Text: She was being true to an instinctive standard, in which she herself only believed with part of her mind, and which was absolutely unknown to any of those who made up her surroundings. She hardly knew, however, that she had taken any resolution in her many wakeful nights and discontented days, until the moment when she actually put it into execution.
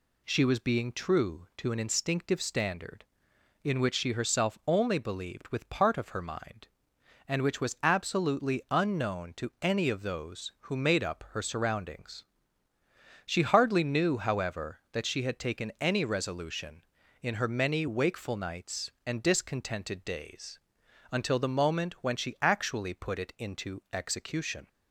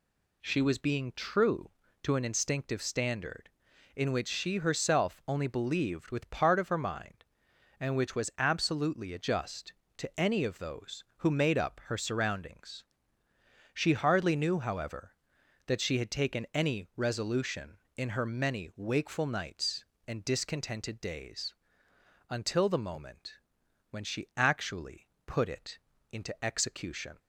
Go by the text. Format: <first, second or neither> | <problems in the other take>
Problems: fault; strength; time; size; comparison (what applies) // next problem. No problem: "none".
first | says "adjust" for "unknown"; at 9.1 s // pauses between "moment" and "when"; noticeable; at 23.3 s; 0.54 s long // pauses between "actually" and "put"; slight; at 25.0 s; 0.18 s long // pauses between "it" and "into"; slight; at 25.7 s; 0.34 s long